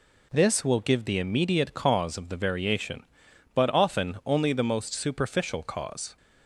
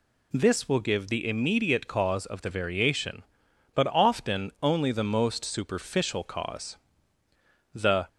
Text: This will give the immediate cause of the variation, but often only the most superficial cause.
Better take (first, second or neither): first